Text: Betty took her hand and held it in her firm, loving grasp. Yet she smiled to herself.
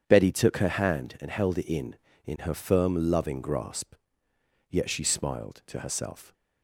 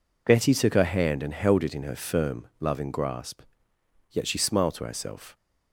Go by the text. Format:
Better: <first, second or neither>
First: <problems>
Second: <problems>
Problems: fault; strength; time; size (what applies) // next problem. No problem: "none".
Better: second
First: starts louder than the rest; strong; until 1.0 s; 8 dB // says "in" twice; at 2.2 s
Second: none